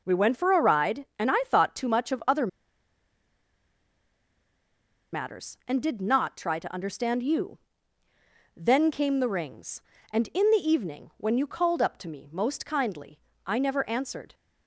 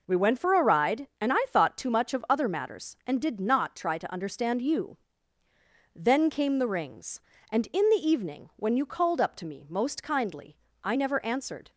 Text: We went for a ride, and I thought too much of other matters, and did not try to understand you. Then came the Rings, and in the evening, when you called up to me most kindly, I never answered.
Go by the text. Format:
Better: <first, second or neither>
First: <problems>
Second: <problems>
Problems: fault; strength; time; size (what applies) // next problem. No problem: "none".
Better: second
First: pauses between "other" and "matters"; strong; at 2.4 s; 2.6 s long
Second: none